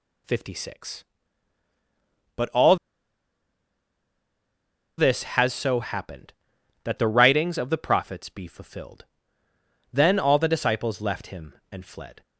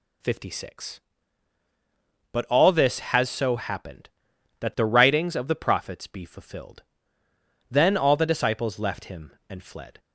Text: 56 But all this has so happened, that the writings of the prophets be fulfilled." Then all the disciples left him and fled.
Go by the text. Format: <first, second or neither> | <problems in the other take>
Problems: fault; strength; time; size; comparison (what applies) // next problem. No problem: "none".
second | pauses between "all" and "this"; strong; at 2.7 s; 2.2 s long